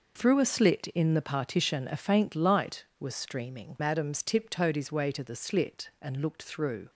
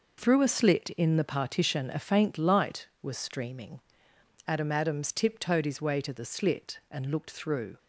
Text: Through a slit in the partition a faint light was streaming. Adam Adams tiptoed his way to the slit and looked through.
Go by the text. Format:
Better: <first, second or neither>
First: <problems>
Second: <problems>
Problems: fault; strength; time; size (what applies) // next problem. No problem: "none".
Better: second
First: skips "Adam"; at 3.7 s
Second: none